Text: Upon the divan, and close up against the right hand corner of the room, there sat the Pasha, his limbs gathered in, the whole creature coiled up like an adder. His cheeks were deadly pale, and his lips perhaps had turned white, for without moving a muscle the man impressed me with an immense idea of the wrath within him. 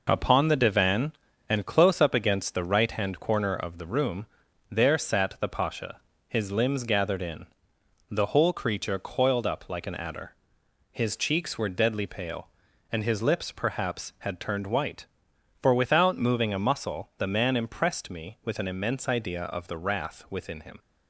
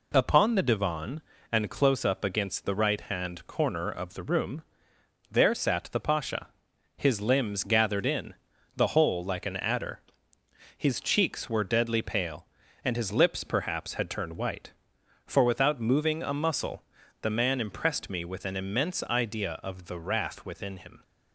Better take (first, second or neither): first